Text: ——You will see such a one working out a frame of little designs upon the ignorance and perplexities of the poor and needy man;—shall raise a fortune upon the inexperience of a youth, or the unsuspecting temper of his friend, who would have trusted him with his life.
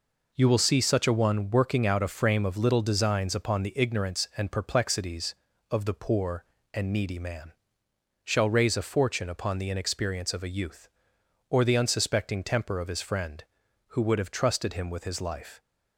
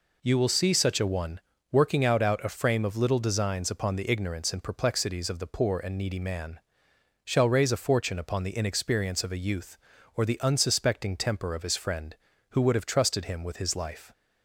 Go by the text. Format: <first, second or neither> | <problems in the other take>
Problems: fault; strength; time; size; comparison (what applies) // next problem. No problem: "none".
first | pauses between "one" and "working"; slight; at 1.3 s; 0.30 s long // says "out" twice; at 2.2 s